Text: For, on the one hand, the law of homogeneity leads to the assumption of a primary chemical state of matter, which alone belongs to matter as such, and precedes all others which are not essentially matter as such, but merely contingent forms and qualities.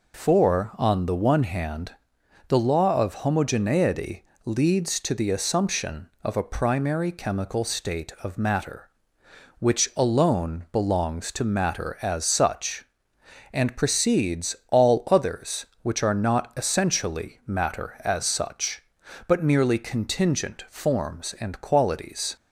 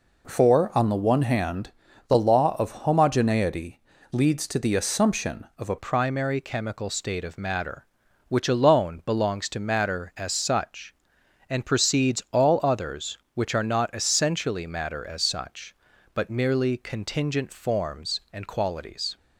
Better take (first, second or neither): first